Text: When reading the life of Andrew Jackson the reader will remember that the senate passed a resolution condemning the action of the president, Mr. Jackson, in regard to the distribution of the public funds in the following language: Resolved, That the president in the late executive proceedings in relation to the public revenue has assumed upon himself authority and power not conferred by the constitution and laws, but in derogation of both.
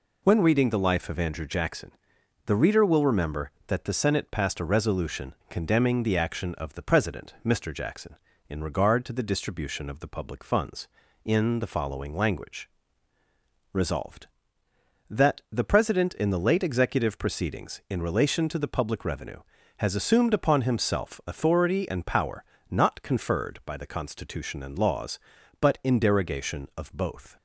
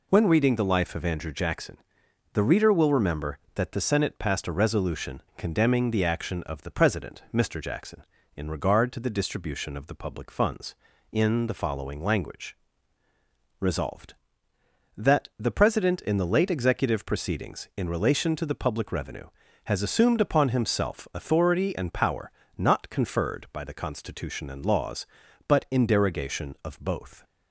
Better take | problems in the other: neither | pauses between "Jackson" and "the"; noticeable; the same in both // pauses between "resolution" and "condemning"; slight; the same in both // pauses between "power" and "not"; slight; the same in both

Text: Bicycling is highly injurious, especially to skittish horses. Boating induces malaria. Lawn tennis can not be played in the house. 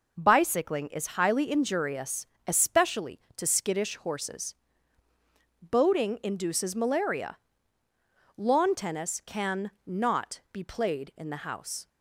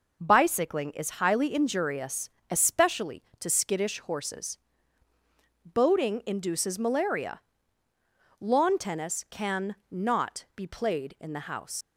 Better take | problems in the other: first | leaves "house" unfinished; at 11.8 s; 105 ms

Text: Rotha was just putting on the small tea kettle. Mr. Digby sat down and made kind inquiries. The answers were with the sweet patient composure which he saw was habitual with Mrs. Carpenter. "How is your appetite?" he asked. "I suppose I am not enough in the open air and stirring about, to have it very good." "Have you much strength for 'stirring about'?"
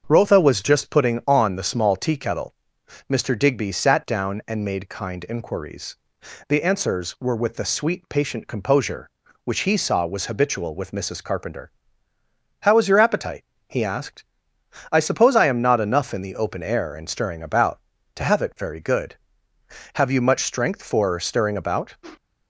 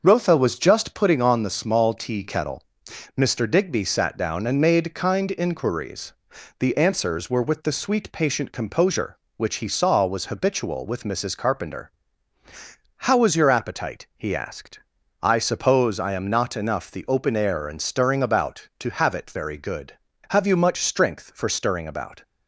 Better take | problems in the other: first | starts louder than the rest; noticeable; until 1.0 s; 6 dB; also in the first // skips "in"; at 16.8 s

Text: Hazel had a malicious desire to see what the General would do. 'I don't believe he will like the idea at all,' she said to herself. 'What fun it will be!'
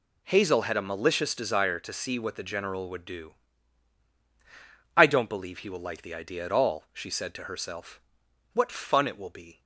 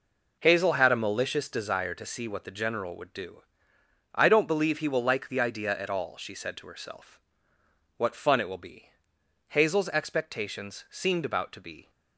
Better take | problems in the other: first | goes on to say "Hazel's expectations seemed about to be"; strong; from 9.4 s on; 2.4 s long

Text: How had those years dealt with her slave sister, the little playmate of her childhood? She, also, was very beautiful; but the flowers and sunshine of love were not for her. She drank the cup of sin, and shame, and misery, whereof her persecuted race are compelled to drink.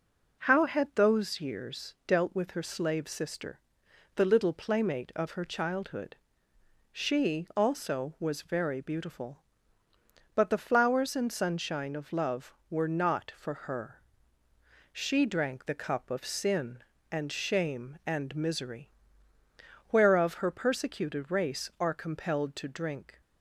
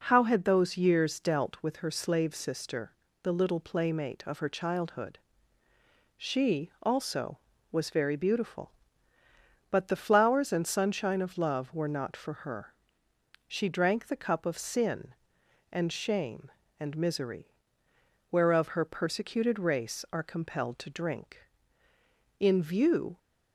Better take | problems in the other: first | goes on to say "In view"; noticeable; from 22.3 s on; 0.78 s long

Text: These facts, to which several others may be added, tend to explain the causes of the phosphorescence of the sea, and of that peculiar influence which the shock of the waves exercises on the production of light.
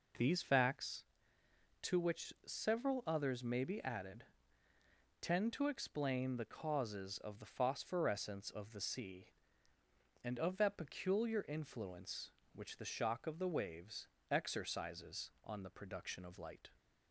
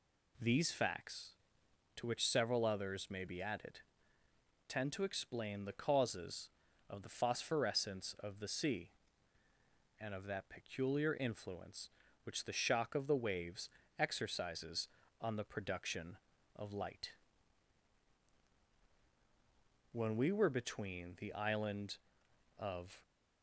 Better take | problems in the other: first | pauses between "waves" and "exercises"; slight; at 13.6 s; 0.28 s long; slight in the first // goes on to say "When we were between the island of"; strong; from 19.9 s on; 3.0 s long

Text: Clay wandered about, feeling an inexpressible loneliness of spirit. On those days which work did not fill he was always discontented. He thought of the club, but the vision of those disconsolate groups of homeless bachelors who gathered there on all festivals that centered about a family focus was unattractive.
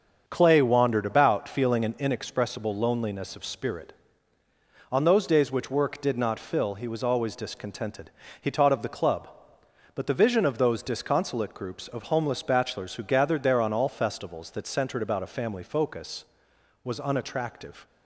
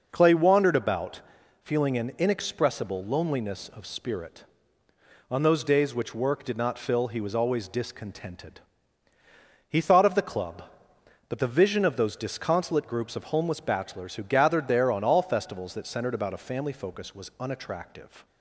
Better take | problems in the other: second | starts louder than the rest; until 1.2 s; 6.5 dB // says "taught" for "thought"; at 8.4 s

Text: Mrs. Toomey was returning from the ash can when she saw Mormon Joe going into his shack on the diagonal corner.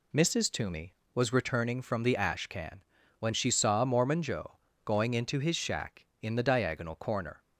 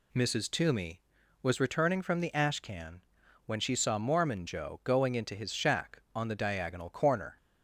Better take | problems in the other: second | pauses between "can" and "when"; slight; at 2.8 s; 0.36 s long; noticeable in the second // pauses between "Joe" and "going"; slight; at 4.5 s; 0.28 s long // says "in" for "on"; at 6.2 s

